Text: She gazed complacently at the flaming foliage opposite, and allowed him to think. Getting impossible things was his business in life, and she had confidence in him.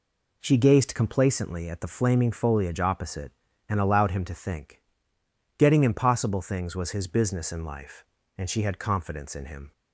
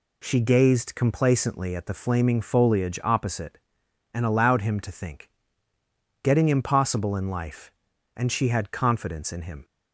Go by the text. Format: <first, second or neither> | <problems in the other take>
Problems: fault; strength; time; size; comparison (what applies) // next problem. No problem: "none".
first | skips "things was his business"; at 7.1 s